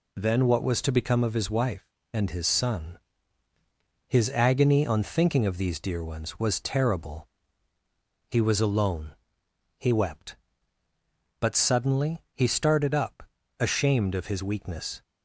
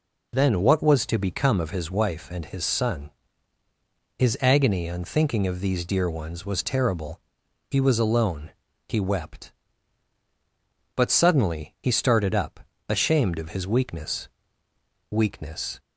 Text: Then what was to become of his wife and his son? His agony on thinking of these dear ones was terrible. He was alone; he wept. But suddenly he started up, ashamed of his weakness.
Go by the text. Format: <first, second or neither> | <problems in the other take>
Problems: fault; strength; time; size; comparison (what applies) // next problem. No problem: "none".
first | says "weakness" twice; at 15.0 s